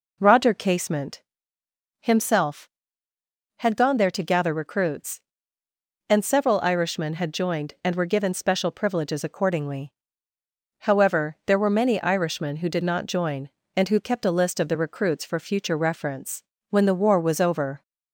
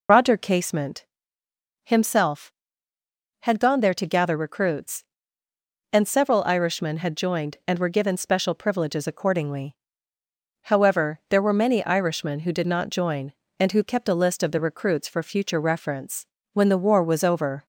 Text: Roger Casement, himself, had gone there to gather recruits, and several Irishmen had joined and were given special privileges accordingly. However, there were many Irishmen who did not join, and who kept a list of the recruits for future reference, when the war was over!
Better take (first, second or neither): first